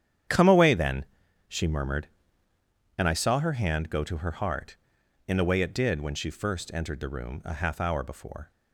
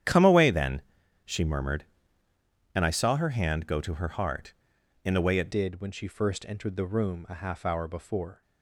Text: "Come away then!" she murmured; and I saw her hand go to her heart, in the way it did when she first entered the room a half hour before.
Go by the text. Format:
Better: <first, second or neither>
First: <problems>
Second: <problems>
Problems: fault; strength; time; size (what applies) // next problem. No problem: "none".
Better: first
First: starts louder than the rest; strong; until 1.7 s; 9.5 dB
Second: starts louder than the rest; strong; until 1.4 s; 10 dB // changes voice at "did"; from 5.5 s on; 2.9 s long